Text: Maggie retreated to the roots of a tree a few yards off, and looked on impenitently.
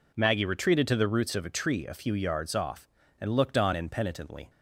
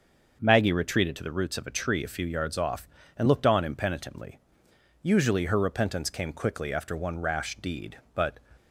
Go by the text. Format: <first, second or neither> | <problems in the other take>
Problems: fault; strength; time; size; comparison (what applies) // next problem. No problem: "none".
first | starts louder than the rest; until 1.4 s; 6.5 dB // goes on to say "Usually her repentance came quickly after one rash deed but"; strong; from 5.0 s on; 3.3 s long